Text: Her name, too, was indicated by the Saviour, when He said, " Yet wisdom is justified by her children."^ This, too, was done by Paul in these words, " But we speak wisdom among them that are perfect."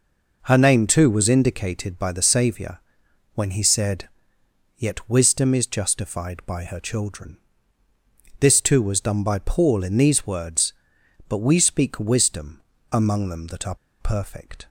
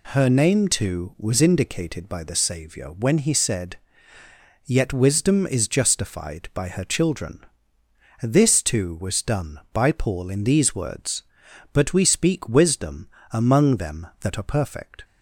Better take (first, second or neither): second